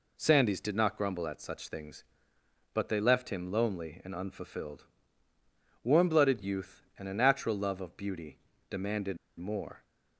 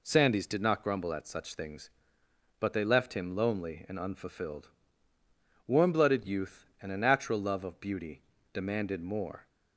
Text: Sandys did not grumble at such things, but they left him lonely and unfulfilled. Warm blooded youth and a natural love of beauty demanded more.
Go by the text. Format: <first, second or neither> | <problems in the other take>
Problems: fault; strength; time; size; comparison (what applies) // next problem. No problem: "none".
second | pauses between "beauty" and "demanded"; slight; at 8.3 s; 0.32 s long; slight in the second // pauses between "demanded" and "more"; slight; at 9.1 s; 0.21 s long